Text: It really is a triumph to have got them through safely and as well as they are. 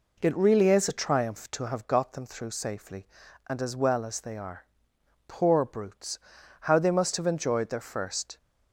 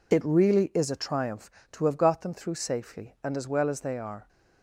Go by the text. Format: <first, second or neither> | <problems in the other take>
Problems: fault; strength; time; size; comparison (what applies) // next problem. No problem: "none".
second | goes on to say "Poor brutes how they must have enjoyed their first"; strong; from 5.2 s on; 3.1 s long